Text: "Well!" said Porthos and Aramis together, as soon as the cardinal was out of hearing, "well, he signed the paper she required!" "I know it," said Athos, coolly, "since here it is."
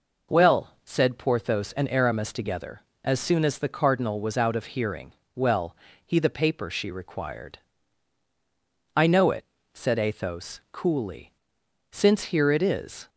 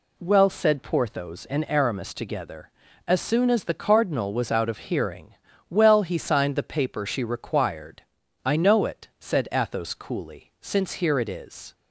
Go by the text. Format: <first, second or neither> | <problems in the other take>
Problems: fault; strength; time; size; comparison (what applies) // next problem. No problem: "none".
second | skips "signed"; at 6.1 s